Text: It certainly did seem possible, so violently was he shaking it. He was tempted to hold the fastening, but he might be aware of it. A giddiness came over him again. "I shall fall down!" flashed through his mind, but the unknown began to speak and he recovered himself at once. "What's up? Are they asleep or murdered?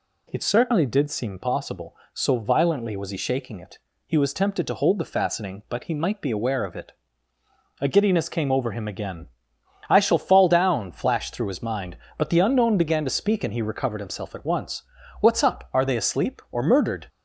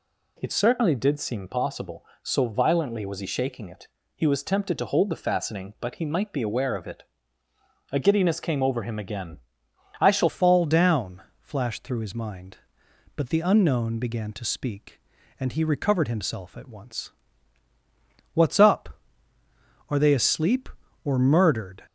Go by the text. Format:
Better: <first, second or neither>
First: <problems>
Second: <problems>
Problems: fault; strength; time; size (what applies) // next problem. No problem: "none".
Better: first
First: none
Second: changes voice at "fall"; from 10.2 s on; 11.6 s long